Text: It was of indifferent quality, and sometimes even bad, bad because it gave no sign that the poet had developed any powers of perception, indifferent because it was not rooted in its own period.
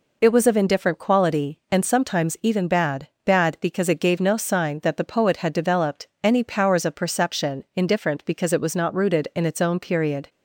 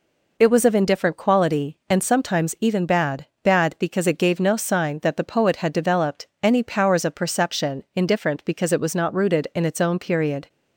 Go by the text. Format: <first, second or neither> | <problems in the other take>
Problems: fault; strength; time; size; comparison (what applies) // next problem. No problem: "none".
neither | none